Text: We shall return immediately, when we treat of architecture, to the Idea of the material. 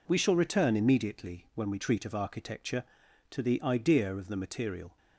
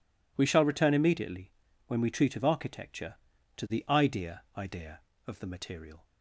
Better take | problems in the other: first | says "Idea" twice; at 4.5 s

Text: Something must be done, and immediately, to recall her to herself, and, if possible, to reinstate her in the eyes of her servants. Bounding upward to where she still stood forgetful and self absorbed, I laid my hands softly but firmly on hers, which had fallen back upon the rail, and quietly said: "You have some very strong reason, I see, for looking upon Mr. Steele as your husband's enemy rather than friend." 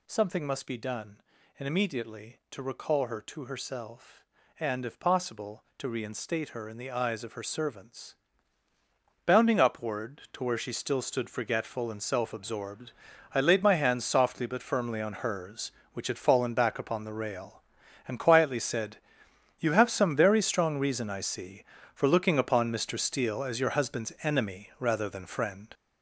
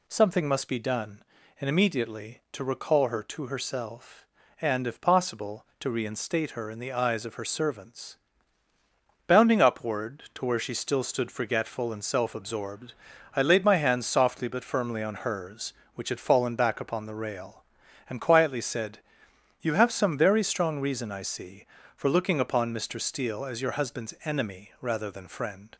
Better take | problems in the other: second | gets louder; throughout; 7 dB

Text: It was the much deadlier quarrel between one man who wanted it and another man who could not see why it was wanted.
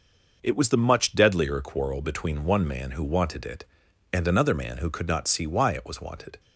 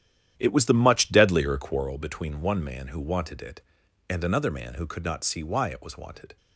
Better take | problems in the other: first | starts louder than the rest; strong; until 2.0 s; 10.5 dB

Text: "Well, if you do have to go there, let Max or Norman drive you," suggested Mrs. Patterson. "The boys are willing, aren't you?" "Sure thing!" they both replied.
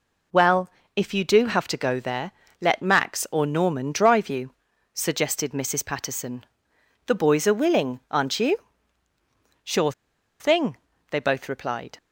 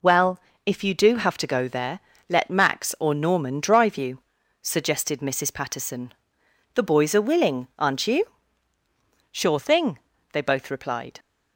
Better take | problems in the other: second | pauses between "Sure" and "thing"; noticeable; at 9.9 s; 0.48 s long

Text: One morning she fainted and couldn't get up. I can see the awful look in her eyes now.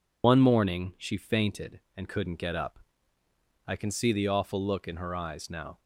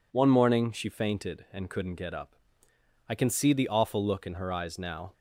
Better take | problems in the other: second | loses the start of "One"; at 0.2 s; 55 ms

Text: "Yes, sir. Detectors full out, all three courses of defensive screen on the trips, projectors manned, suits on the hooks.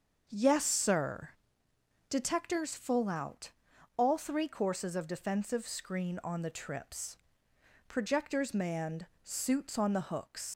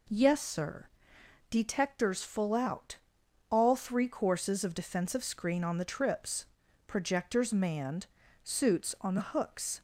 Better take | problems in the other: second | starts louder than the rest; until 1.2 s; 6.5 dB // leaves "hooks" unfinished; at 10.5 s; 110 ms

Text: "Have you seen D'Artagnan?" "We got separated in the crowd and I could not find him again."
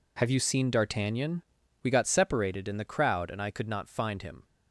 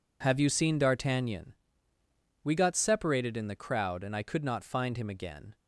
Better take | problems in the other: second | stops before "again"; at 4.4 s

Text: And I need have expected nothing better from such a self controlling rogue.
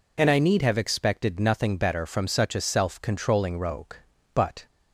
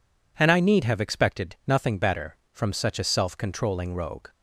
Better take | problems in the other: second | goes on to say "But"; slight; from 4.3 s on; 0.30 s long

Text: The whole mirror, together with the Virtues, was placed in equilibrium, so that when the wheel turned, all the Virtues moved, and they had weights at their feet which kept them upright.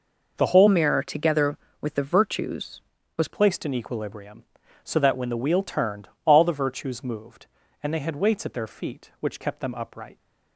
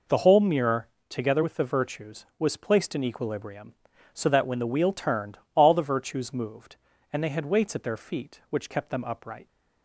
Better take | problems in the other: second | changes voice from "mirror" to "was"; from 0.6 to 3.2 s; 2.6 s long

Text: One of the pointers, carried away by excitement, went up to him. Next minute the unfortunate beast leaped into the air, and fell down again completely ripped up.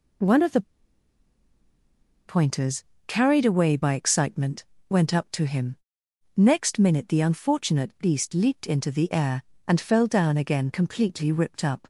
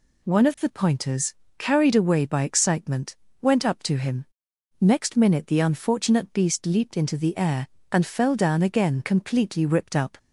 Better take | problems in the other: second | pauses between "the" and "pointers"; strong; at 0.6 s; 1.6 s long

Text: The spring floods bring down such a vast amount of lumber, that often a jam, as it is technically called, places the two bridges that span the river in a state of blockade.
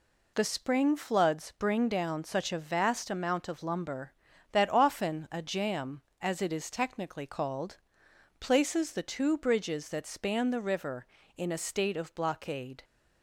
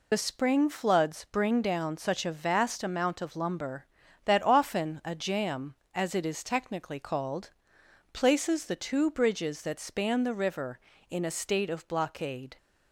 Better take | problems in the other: first | loses the start of "The"; at 0.1 s; 30 ms

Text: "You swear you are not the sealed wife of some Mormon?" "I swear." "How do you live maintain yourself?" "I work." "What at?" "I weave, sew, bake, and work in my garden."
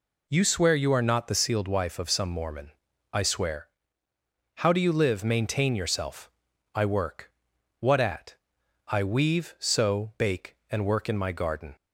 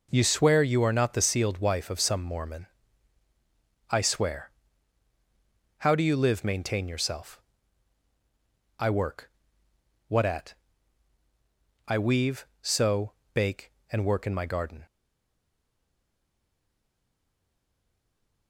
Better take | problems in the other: first | stays silent after the last word; strong; from 14.8 s on; 3.6 s long

